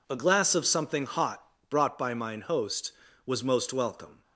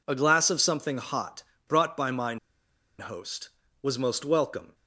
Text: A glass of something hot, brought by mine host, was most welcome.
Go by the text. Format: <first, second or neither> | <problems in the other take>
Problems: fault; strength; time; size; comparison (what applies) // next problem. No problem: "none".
first | pauses between "mine" and "host"; noticeable; at 2.3 s; 0.62 s long